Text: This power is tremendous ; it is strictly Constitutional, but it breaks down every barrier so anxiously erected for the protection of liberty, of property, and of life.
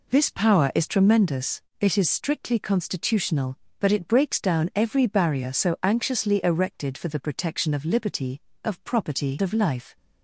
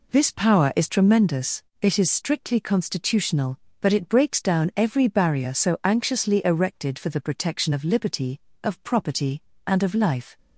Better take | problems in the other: second | skips "and"; at 9.4 s

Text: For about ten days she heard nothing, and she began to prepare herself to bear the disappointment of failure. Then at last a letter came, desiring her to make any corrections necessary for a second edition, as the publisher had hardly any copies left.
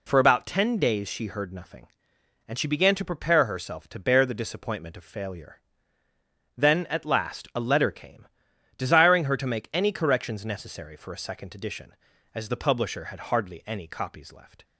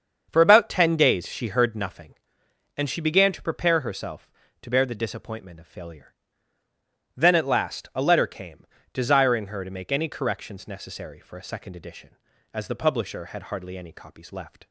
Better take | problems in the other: first | starts louder than the rest; until 1.8 s; 7 dB

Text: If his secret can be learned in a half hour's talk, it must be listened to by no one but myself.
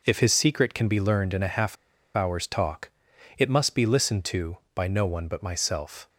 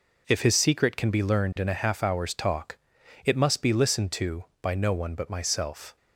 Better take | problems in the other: second | pauses between "half" and "hour's"; at 1.7 s; 0.41 s long

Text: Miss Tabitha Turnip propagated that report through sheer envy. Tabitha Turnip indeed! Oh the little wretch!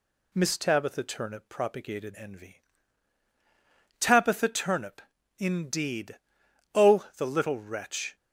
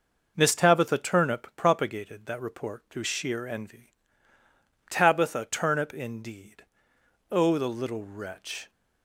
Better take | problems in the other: second | skips "that report through sheer"; at 2.1 s // pauses between "Turnip" and "indeed"; at 5.0 s; 0.38 s long

